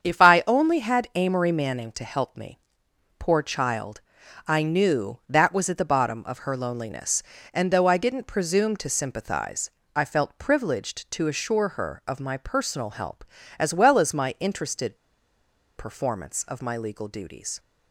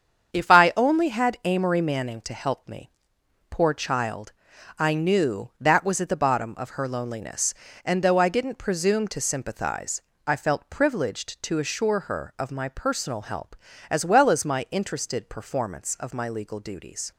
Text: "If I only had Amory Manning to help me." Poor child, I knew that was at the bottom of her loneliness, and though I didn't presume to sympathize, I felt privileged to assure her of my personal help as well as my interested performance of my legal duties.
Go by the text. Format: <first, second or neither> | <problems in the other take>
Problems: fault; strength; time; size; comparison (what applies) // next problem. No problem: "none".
second | starts louder than the rest; strong; until 1.0 s; 7.5 dB; strong in the second // pauses between "interested" and "performance"; noticeable; at 14.9 s; 0.80 s long